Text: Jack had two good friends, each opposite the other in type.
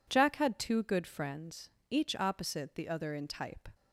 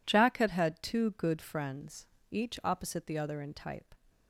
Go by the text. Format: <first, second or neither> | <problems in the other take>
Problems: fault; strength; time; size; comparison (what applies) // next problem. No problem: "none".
first | says "had" twice; at 0.4 s